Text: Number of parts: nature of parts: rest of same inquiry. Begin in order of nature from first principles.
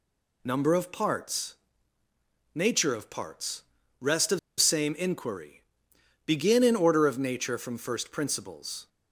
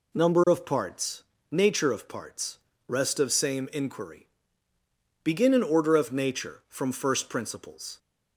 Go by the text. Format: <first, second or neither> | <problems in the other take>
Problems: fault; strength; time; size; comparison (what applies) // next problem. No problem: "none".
second | pauses between "of" and "same"; slight; at 4.3 s; 0.20 s long